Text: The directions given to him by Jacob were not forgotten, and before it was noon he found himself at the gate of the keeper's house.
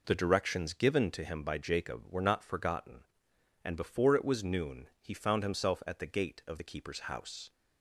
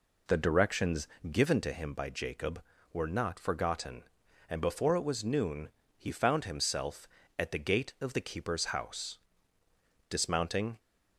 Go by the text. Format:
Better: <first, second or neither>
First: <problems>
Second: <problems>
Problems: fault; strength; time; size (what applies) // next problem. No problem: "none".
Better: first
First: none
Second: pauses between "directions" and "given"; slight; at 1.0 s; 0.24 s long // pauses between "noon" and "he"; slight; at 5.6 s; 0.28 s long // goes on to say "Dismounting"; noticeable; from 10.0 s on; 0.70 s long